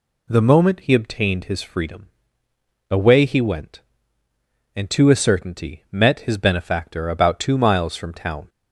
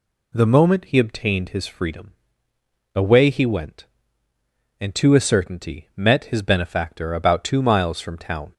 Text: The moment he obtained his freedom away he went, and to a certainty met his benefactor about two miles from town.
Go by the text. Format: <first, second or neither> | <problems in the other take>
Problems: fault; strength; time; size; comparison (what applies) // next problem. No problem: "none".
neither | pauses between "freedom" and "away"; noticeable; the same in both